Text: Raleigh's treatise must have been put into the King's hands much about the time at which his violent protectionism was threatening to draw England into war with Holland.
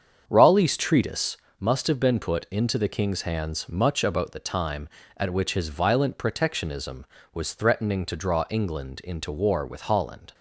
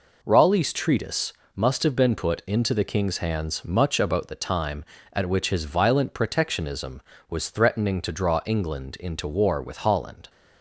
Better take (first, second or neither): second